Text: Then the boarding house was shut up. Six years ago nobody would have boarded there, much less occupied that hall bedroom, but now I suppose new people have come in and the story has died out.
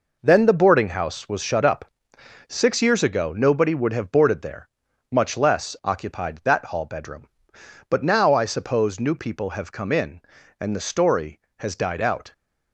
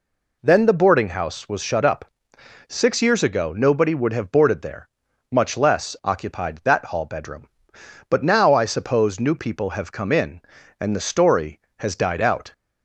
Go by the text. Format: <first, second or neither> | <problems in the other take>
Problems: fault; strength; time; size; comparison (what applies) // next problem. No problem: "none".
second | gets quieter; strong; throughout; 7.5 dB